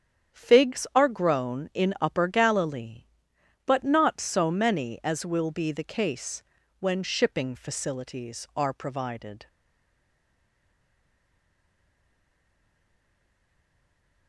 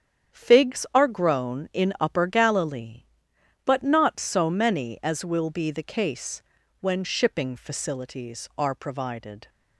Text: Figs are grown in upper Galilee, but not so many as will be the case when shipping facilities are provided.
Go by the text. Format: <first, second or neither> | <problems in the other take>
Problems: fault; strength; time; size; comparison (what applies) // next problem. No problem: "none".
second | starts louder than the rest; strong; until 1.4 s; 8.5 dB; strong in the second // pauses between "case" and "when"; slight; at 6.4 s; 0.34 s long; also in the second // stays silent after the last word; strong; from 9.4 s on; 4.8 s long